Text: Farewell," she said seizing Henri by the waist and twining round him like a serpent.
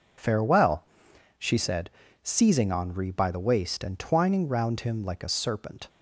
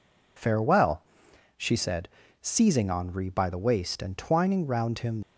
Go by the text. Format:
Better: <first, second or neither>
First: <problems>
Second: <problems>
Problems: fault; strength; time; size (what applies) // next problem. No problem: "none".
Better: first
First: pauses between "said" and "seizing"; slight; at 1.8 s; 0.32 s long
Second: pauses between "said" and "seizing"; slight; at 2.0 s; 0.32 s long // stops before "like a serpent"; at 5.2 s